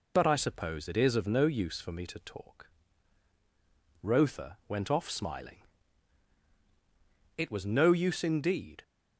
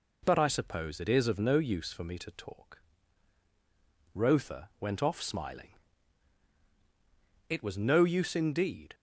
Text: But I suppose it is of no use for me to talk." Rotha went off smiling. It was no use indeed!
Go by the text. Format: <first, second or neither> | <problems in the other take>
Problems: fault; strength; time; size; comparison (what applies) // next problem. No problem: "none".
second | loses the start of "But"; at 0.1 s; 35 ms